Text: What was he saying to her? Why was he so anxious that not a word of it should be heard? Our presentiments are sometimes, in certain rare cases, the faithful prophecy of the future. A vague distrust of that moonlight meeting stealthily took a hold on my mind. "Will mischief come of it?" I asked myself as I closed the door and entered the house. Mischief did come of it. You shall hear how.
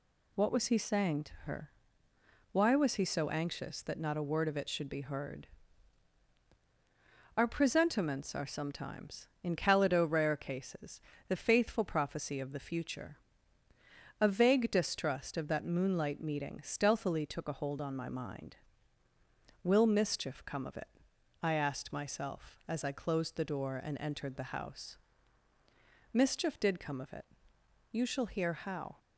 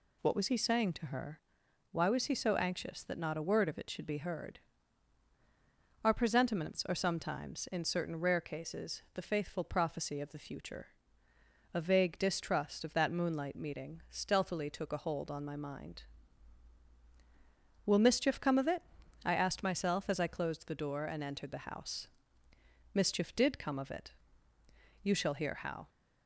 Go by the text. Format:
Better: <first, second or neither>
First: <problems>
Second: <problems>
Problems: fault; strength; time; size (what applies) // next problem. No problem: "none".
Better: second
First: says "calido" for "certain"; at 9.5 s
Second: none